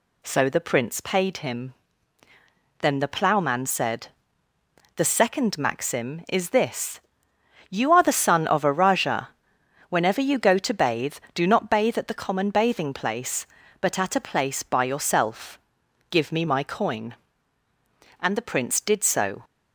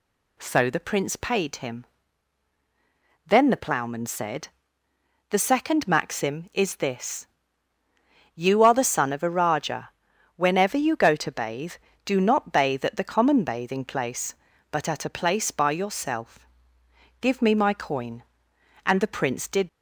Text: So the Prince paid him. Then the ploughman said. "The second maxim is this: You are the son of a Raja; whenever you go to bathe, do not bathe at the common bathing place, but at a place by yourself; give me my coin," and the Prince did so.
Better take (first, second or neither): first